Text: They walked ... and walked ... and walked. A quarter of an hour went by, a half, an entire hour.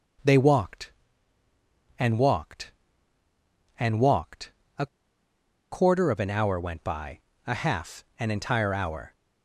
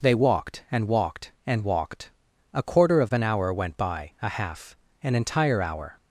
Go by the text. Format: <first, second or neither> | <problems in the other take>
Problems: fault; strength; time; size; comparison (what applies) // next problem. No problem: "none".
second | pauses between "A" and "quarter"; noticeable; at 4.8 s; 0.84 s long